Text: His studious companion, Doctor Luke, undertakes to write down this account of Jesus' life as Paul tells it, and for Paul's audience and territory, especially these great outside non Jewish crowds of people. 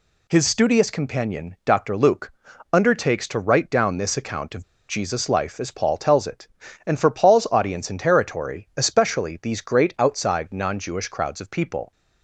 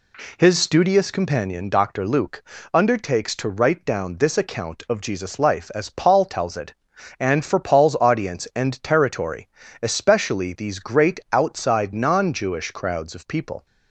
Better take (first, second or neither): second